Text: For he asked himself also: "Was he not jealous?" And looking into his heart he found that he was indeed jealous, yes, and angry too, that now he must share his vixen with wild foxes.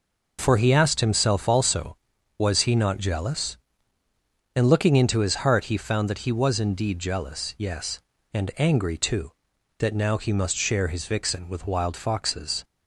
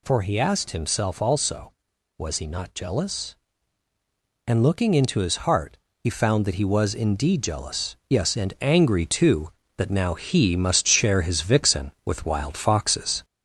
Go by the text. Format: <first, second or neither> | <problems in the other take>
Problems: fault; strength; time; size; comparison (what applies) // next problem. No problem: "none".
first | gets louder; slight; throughout; 3 dB // pauses between "heart" and "he"; slight; at 5.7 s; 0.20 s long